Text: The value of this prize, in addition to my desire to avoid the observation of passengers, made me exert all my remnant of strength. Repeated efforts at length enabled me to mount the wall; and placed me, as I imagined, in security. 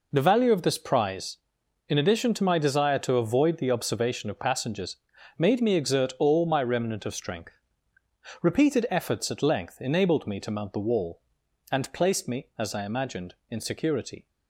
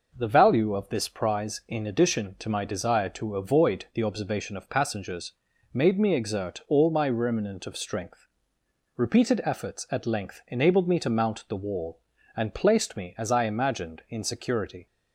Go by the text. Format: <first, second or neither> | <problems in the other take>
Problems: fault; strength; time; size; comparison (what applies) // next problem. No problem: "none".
neither | none